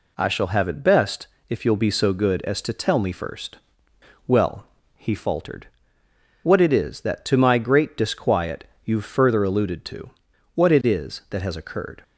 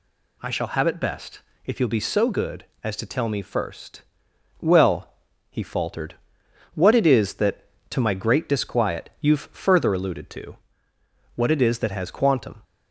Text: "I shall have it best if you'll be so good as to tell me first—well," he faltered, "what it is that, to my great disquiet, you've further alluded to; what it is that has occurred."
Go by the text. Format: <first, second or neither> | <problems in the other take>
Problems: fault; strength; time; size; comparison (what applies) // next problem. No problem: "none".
first | pauses between "best" and "if"; slight; at 1.4 s; 0.24 s long; slight in the first // says "quantum" for "occurred"; at 12.1 s